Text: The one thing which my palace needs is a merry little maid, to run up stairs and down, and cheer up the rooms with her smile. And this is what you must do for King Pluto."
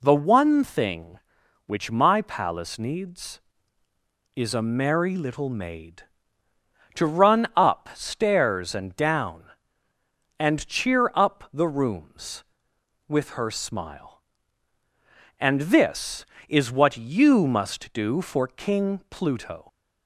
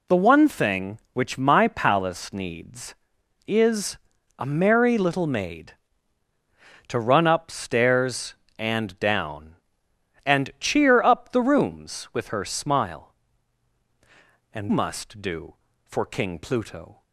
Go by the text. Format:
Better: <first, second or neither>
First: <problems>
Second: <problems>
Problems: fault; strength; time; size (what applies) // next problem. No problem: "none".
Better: first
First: none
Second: pauses between "is" and "a"; at 3.9 s; 0.40 s long // skips "this is what you"; at 14.6 s